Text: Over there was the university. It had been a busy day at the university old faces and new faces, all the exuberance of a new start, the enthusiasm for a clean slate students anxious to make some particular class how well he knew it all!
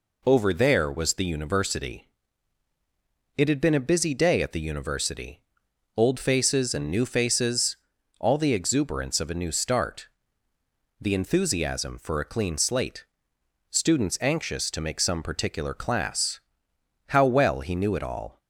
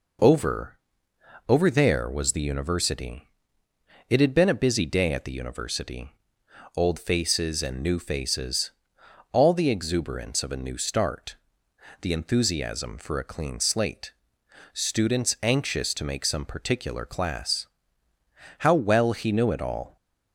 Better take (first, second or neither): first